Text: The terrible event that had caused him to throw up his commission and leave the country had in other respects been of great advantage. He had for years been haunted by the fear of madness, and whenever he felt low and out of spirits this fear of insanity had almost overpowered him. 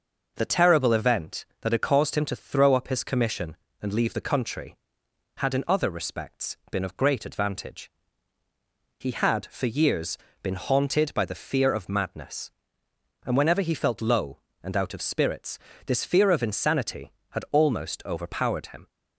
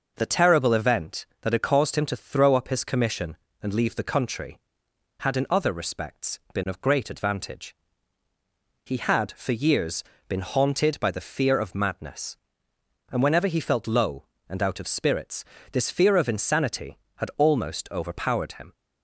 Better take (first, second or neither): neither